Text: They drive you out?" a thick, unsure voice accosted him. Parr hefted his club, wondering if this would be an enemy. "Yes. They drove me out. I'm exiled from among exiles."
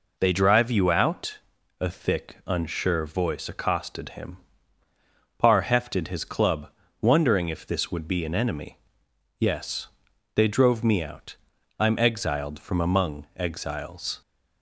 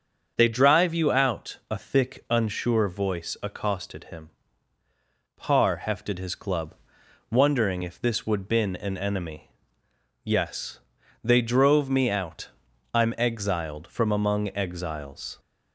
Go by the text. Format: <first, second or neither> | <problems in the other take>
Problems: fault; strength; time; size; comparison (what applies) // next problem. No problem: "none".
first | starts louder than the rest; until 1.3 s; 6.5 dB // says "been" for "be"; at 8.4 s